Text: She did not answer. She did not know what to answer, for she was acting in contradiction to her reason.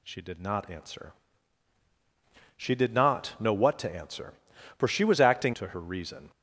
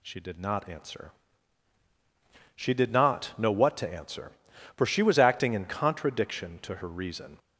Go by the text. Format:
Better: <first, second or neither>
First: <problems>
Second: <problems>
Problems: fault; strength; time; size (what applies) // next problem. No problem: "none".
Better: second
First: skips "in contradiction"; at 5.5 s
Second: none